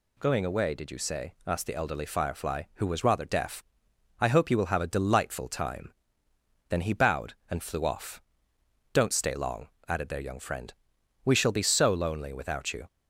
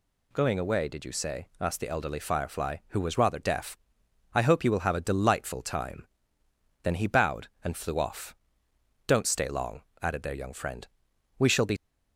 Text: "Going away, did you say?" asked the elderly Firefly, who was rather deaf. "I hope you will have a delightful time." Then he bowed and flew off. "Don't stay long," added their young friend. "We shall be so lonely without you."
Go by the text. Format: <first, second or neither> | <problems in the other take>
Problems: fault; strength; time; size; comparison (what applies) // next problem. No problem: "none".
first | stops before "so lonely without you"; at 11.7 s